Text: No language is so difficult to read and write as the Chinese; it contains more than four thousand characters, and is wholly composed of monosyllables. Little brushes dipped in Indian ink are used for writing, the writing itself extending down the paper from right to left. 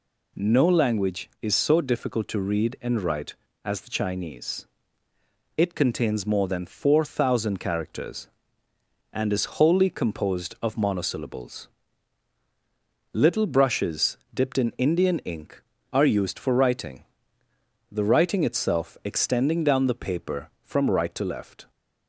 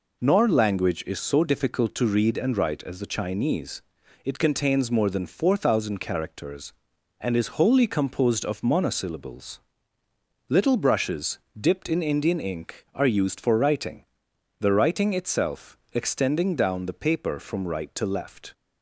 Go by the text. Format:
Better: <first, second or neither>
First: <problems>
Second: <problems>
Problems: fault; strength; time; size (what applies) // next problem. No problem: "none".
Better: first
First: pauses between "brushes" and "dipped"; slight; at 14.1 s; 0.18 s long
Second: says "Nor" for "No"; at 0.2 s // pauses between "brushes" and "dipped"; slight; at 11.3 s; 0.20 s long